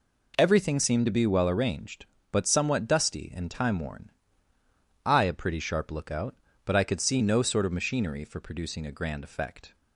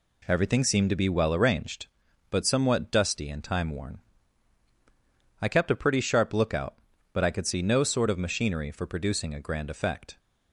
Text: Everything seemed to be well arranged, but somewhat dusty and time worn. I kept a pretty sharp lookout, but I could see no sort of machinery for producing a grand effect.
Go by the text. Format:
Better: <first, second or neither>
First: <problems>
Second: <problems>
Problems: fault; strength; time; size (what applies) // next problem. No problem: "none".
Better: second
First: skips "kept"; at 5.2 s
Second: none